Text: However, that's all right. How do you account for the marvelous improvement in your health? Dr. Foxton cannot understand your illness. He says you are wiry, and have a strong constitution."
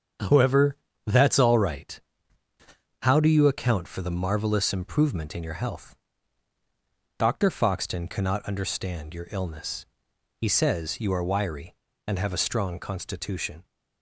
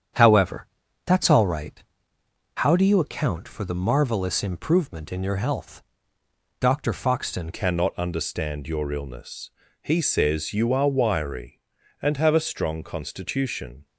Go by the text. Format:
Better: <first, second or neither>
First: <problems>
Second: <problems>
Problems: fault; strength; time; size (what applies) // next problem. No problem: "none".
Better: first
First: starts louder than the rest; strong; until 1.5 s; 7.5 dB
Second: starts louder than the rest; strong; until 1.5 s; 8.5 dB // changes voice at "cannot"; from 7.5 s on; 6.3 s long